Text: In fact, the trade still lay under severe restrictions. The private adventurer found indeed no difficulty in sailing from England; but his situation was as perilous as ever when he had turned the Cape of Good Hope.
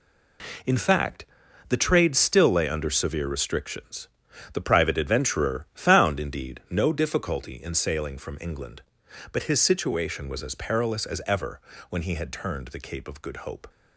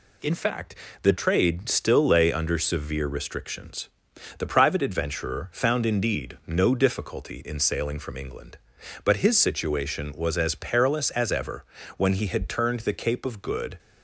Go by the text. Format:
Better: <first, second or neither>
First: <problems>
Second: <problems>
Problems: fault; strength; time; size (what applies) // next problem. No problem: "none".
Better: first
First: pauses between "ever" and "when"; slight; at 11.6 s; 0.30 s long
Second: pauses between "ever" and "when"; slight; at 11.6 s; 0.32 s long // stops before "Hope"; at 13.7 s